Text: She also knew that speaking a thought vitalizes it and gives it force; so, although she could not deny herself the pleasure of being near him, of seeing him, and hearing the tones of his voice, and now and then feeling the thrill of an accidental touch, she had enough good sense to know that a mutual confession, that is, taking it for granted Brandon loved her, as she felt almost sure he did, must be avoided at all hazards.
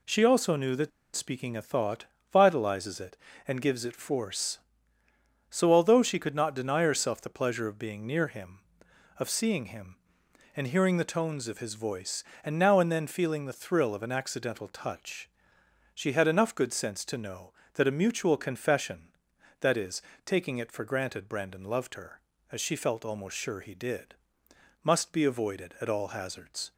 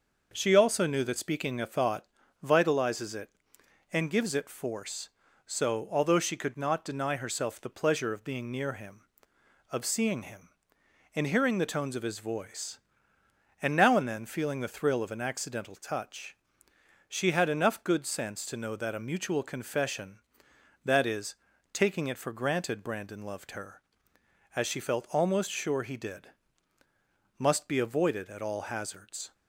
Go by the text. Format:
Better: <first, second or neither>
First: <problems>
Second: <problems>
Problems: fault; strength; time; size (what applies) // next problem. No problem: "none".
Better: second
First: pauses between "that" and "speaking"; slight; at 0.9 s; 0.26 s long // pauses between "thought" and "vitalizes"; slight; at 2.0 s; 0.26 s long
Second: pauses between "thought" and "vitalizes"; slight; at 2.0 s; 0.36 s long